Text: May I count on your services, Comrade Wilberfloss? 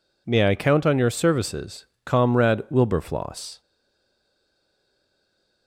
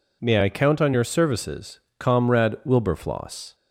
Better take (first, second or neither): second